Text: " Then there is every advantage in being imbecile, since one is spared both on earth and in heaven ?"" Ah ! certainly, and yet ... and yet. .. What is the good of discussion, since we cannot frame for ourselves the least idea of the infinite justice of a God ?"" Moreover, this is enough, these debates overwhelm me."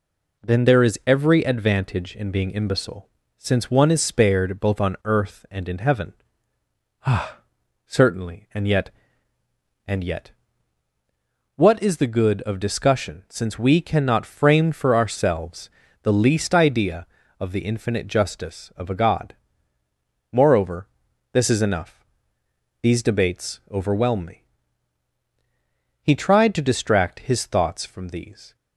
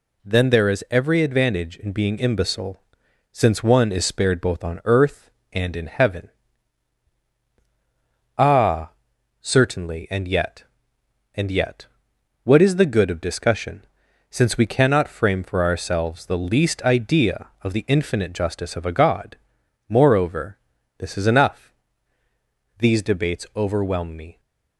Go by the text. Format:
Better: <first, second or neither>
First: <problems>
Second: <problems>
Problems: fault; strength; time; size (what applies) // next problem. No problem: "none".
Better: second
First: pauses between "ourselves" and "the"; slight; at 15.6 s; 0.32 s long // goes on to say "He tried to distract his thoughts from these"; strong; from 26.0 s on; 2.5 s long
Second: none